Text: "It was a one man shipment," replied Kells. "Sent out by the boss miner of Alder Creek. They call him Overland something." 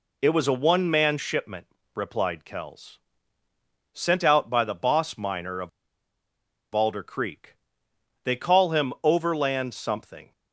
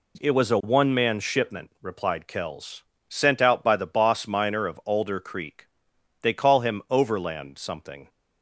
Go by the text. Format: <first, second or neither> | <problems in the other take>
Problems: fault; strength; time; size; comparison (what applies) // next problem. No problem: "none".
second | pauses between "of" and "Alder"; at 5.6 s; 1.0 s long